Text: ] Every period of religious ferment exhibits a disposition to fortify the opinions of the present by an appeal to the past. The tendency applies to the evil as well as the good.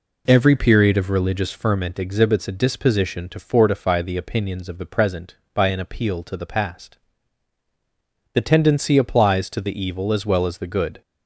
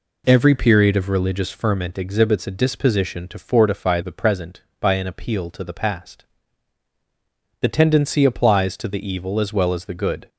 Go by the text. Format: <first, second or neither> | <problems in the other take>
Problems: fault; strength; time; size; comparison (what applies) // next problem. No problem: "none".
first | skips "the opinions of"; at 4.0 s